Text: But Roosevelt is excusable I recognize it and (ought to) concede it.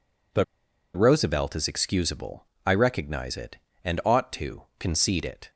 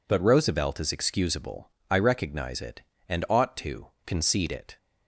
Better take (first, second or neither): second